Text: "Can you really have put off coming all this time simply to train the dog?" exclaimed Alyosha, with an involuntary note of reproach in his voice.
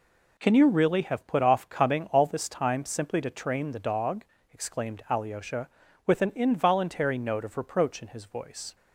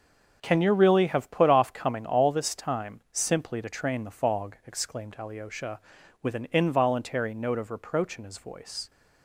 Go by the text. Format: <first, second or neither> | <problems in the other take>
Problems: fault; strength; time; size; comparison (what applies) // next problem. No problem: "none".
first | starts louder than the rest; until 1.4 s; 6.5 dB // says "fog" for "dog"; at 4.1 s